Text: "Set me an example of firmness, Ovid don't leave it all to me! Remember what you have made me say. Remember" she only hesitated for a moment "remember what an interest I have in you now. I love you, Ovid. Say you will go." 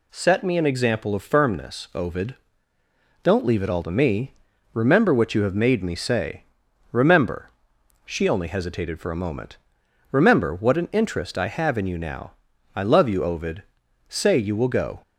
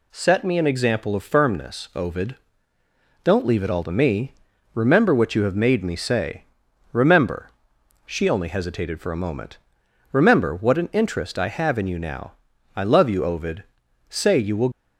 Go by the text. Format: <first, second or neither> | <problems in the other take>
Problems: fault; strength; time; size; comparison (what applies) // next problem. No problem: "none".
first | pauses between "Ovid" and "don't"; noticeable; at 2.3 s; 0.86 s long; noticeable in the first // pauses between "Remember" and "she"; noticeable; at 7.5 s; 0.56 s long; noticeable in the first // pauses between "moment" and "remember"; noticeable; at 9.5 s; 0.54 s long; noticeable in the first // stops before "go"; at 14.7 s